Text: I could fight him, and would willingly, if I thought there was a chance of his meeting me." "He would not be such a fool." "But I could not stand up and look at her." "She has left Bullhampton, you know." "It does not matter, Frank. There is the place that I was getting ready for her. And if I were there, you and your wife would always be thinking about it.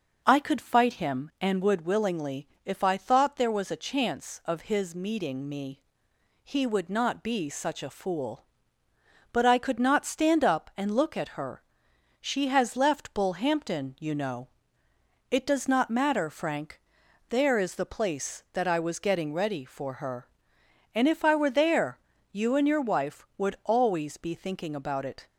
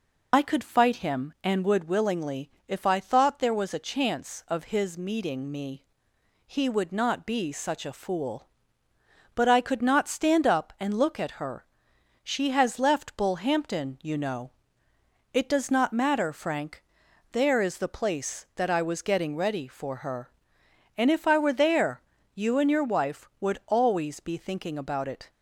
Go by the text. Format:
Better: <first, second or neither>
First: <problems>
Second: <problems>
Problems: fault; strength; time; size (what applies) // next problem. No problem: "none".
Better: first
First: none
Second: loses the start of "I"; at 0.3 s; 60 ms